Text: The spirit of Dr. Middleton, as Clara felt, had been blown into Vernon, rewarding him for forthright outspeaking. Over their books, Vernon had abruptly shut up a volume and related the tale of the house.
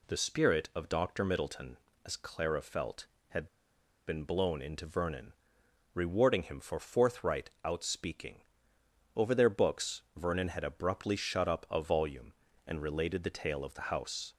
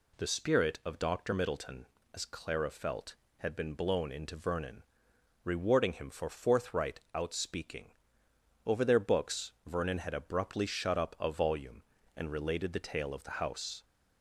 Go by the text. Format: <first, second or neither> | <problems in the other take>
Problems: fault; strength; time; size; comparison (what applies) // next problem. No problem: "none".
second | pauses between "had" and "been"; noticeable; at 3.4 s; 0.61 s long // pauses between "forthright" and "outspeaking"; slight; at 7.4 s; 0.16 s long; slight in the second